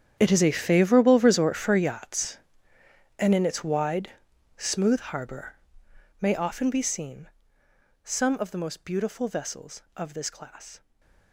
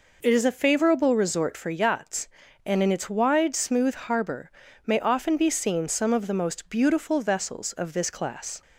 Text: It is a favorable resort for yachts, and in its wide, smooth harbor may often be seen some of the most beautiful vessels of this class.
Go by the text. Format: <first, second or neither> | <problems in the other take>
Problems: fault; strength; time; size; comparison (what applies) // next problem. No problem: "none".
second | gets quieter; strong; throughout; 17 dB // pauses between "harbor" and "may"; noticeable; at 5.5 s; 0.64 s long; slight in the second // pauses between "seen" and "some"; noticeable; at 7.2 s; 0.72 s long // stays silent after the last word; slight; from 10.7 s on; 0.6 s long